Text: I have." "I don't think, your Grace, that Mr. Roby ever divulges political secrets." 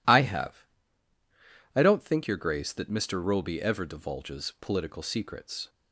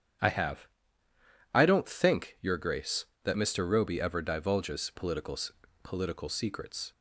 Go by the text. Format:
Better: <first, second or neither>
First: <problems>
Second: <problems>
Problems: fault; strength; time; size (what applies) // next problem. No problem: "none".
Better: first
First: none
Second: starts louder than the rest; strong; until 2.0 s; 9 dB // says "political" twice; at 5.8 s